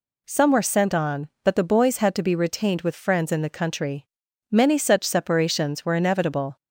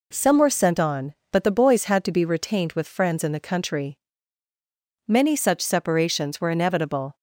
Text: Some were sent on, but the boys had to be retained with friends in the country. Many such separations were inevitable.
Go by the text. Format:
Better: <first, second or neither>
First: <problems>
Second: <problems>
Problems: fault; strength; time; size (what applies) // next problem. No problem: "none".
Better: neither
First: none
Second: none